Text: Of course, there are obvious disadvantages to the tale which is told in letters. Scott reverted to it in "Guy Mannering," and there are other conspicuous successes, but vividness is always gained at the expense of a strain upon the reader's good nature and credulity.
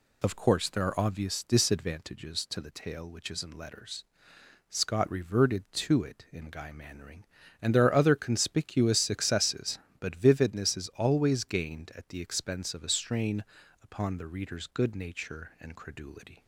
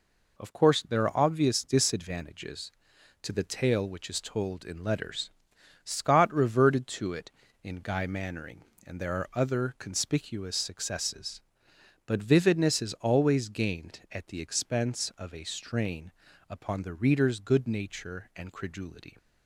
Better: second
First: skips "told"; at 3.4 s // pauses between "strain" and "upon"; at 13.4 s; 0.40 s long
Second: pauses between "strain" and "upon"; at 16.1 s; 0.38 s long

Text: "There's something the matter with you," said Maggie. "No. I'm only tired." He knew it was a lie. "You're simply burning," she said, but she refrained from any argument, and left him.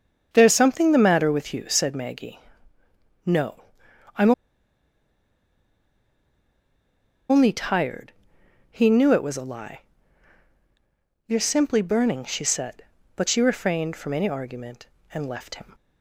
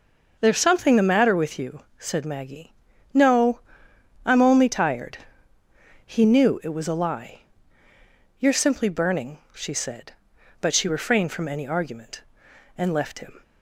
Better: second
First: starts louder than the rest; strong; until 1.3 s; 7.5 dB // pauses between "I'm" and "only"; strong; at 4.3 s; 2.9 s long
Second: none

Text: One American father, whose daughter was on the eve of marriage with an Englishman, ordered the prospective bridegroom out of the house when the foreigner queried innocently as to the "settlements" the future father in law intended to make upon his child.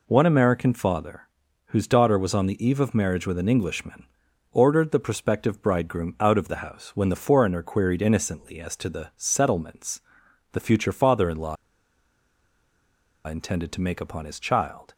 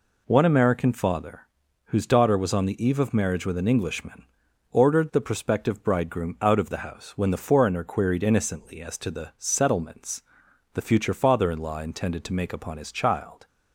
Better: second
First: pauses between "settlements" and "the"; noticeable; at 10.0 s; 0.50 s long // pauses between "law" and "intended"; strong; at 11.5 s; 1.7 s long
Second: pauses between "settlements" and "the"; noticeable; at 10.2 s; 0.50 s long

